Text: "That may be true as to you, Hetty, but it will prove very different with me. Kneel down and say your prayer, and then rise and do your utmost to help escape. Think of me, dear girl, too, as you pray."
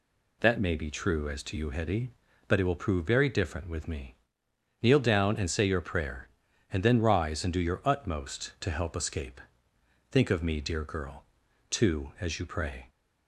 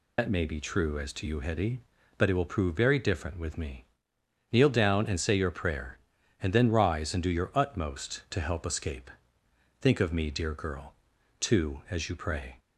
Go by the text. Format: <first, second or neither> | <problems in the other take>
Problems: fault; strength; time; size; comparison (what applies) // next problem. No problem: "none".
first | loses the start of "That"; at 0.1 s; 75 ms